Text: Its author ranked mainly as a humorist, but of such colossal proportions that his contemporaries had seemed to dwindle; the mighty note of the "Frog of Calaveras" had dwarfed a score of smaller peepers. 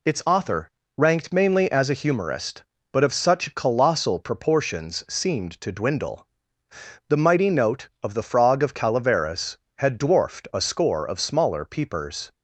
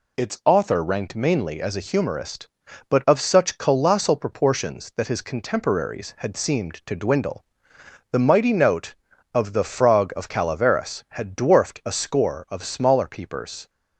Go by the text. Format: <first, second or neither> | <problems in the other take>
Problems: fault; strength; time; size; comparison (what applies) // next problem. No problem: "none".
second | pauses between "author" and "ranked"; slight; at 0.6 s; 0.28 s long // skips "that his contemporaries had"; at 5.0 s